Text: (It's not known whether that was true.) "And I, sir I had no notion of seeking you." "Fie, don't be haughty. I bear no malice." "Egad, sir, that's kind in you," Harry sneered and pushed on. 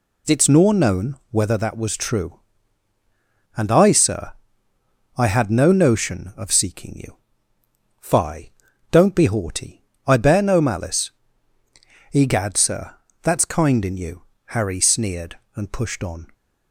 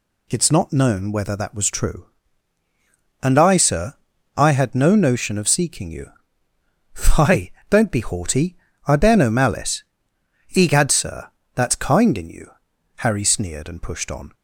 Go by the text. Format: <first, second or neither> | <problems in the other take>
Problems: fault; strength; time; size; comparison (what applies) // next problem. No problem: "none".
second | says "nor" for "not"; at 0.4 s // pauses between "sir" and "I"; noticeable; at 4.3 s; 0.84 s long; also in the second